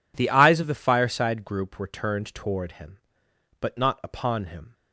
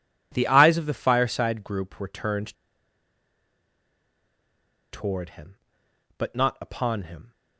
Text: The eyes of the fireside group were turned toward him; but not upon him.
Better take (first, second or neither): first